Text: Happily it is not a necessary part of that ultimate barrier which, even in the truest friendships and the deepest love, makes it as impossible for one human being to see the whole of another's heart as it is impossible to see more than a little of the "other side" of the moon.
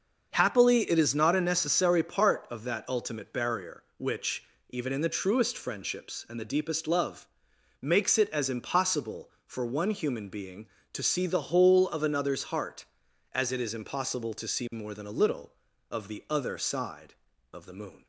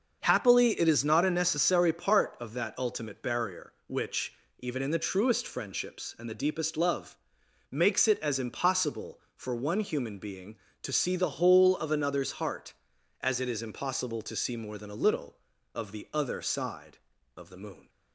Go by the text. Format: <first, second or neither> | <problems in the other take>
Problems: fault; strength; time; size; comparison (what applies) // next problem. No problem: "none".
neither | starts louder than the rest; the same in both